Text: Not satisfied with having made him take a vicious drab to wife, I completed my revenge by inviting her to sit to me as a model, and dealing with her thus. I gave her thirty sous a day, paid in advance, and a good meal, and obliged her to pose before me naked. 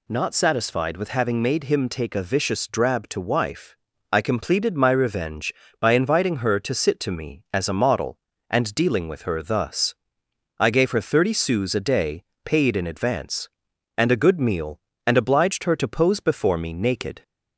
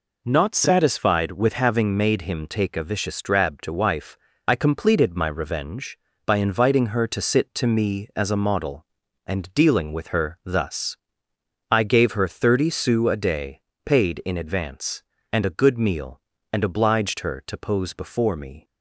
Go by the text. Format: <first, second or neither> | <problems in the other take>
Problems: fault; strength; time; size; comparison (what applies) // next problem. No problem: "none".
first | stops before "naked"; at 18.6 s